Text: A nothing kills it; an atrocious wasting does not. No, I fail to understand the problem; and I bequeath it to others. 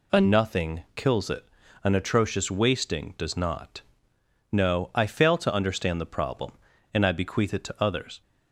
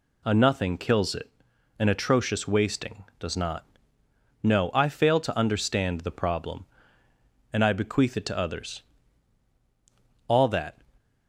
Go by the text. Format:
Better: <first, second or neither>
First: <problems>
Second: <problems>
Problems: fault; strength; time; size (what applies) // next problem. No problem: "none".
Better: first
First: none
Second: goes on to say "All that"; from 10.2 s on; 0.52 s long